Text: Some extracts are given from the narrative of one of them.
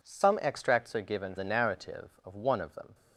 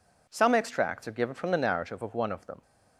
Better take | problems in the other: second | skips "from"; at 1.3 s

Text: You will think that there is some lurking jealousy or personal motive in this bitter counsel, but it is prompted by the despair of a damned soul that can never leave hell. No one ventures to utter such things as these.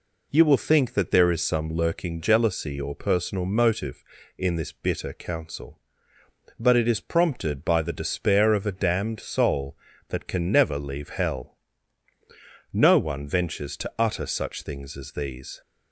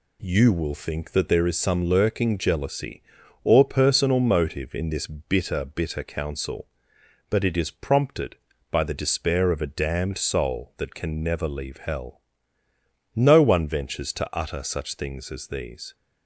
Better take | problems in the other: first | says "bitter" twice; at 5.6 s

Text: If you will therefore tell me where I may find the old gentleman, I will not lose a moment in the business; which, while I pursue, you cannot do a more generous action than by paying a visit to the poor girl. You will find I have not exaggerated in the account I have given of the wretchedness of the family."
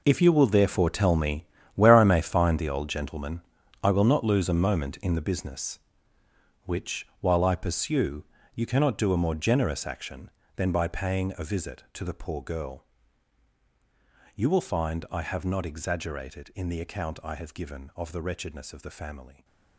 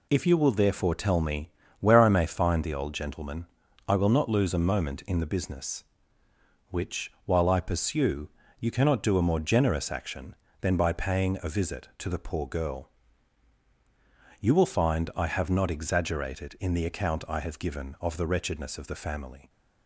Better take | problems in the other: second | gets quieter; strong; throughout; 13.5 dB // pauses between "me" and "where"; slight; at 1.4 s; 0.30 s long; slight in the second

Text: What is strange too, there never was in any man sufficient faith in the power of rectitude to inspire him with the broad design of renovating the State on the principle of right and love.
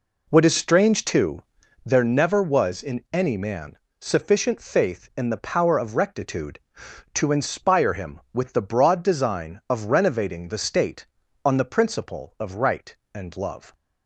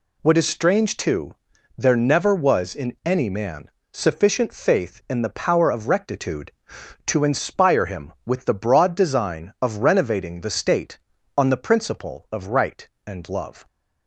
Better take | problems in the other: second | starts louder than the rest; until 2.0 s; 3.5 dB // pauses between "man" and "sufficient"; slight; at 3.7 s; 0.20 s long; slight in the second

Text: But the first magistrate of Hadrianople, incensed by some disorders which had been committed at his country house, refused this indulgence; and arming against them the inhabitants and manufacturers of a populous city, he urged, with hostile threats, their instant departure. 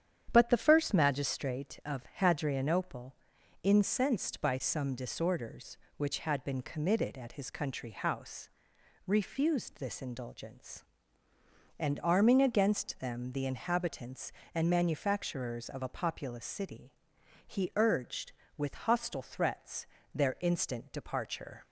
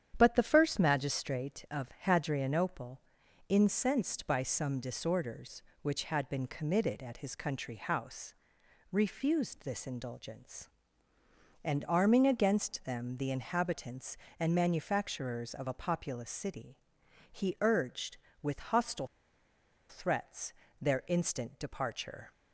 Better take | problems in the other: first | starts louder than the rest; strong; until 1.1 s; 9.5 dB; strong in the first // pauses between "of" and "Hadrianople"; slight; at 1.8 s; 0.16 s long; slight in the first // pauses between "hostile" and "threats"; noticeable; at 19.0 s; 0.82 s long

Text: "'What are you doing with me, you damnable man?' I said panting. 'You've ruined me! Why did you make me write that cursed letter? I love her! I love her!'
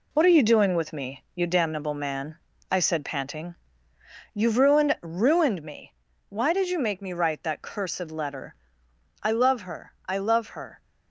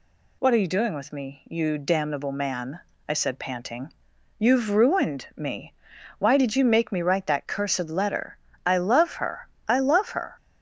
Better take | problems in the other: second | says "ruined" twice; at 5.0 s

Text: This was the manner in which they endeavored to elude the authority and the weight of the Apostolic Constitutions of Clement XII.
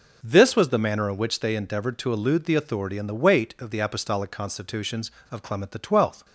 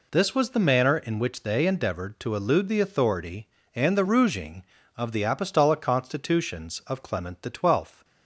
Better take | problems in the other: first | says "rouging" for "weight"; at 4.0 s

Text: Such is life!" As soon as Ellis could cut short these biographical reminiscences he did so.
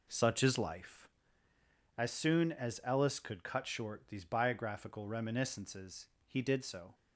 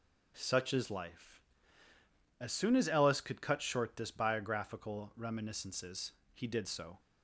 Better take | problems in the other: first | says "this" for "these"; at 3.9 s // pauses between "reminiscences" and "he"; slight; at 6.1 s; 0.22 s long; slight in the first

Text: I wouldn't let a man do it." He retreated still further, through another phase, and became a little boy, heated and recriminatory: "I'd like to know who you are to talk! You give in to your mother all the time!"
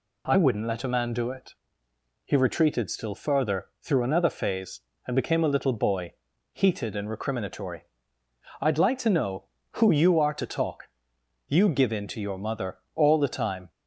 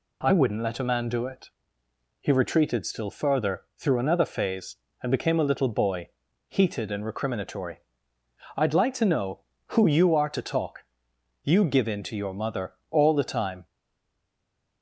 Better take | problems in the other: first | pauses between "mother" and "all"; slight; at 12.7 s; 0.18 s long; slight in the first // stays silent after the last word; noticeable; from 13.6 s on; 1.2 s long

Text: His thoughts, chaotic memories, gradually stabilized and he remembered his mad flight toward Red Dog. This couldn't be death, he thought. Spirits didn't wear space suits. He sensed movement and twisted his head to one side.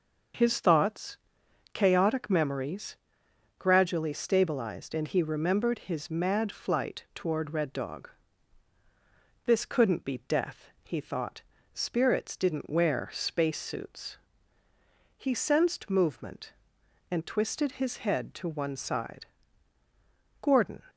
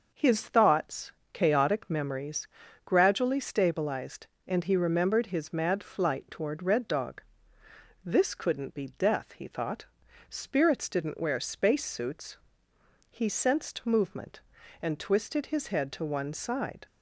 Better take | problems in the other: second | starts louder than the rest; noticeable; until 1.9 s; 6 dB // goes on to say "Gordon"; slight; from 20.4 s on; 0.40 s long

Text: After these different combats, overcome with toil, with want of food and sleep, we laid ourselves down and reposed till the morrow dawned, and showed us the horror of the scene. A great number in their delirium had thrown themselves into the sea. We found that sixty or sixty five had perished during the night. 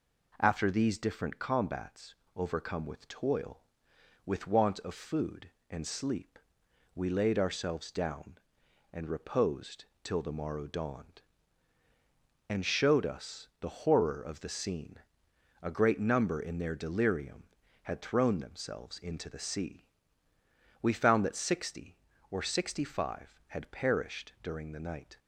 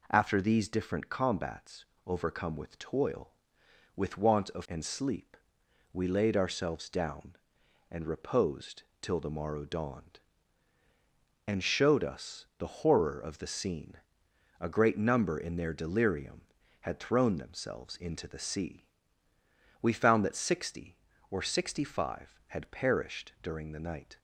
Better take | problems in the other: first | skips "food"; at 4.6 s // pauses between "reposed" and "till"; slight; at 8.8 s; 0.18 s long; slight in the first

